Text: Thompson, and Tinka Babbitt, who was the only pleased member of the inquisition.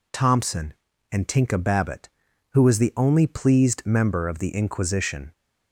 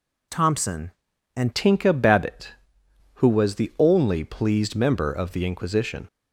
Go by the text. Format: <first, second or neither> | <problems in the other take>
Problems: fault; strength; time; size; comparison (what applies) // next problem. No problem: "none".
first | changes voice at "Tinka"; from 1.5 s on; 4.5 s long